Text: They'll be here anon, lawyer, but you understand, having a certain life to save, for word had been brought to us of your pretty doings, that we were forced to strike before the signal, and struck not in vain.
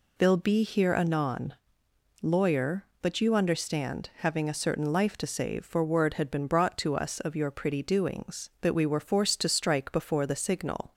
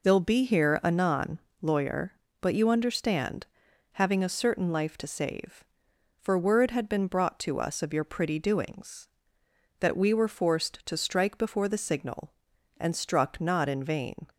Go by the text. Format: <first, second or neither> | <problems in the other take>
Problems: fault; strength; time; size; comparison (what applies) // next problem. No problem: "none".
second | stops before "and struck not in vain"; at 10.9 s